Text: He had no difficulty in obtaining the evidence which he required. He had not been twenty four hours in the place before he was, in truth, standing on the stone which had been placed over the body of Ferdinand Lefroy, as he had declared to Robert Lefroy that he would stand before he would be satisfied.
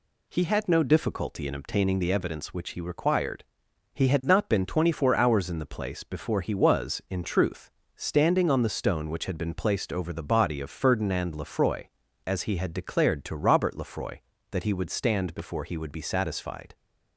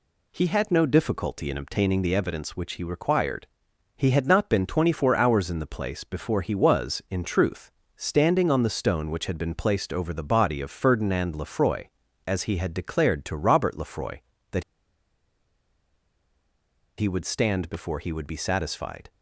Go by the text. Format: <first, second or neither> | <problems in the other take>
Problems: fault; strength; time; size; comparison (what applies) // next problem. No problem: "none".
first | pauses between "that" and "he"; strong; at 14.6 s; 2.3 s long